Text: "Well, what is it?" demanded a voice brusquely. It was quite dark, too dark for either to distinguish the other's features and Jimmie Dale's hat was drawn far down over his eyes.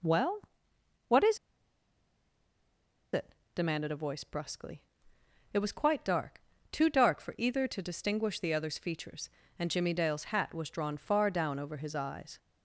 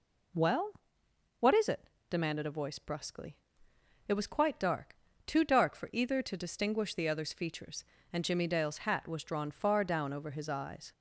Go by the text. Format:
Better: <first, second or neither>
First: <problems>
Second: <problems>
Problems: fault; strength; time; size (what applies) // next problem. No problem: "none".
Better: second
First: pauses between "is" and "it"; strong; at 1.3 s; 1.7 s long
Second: none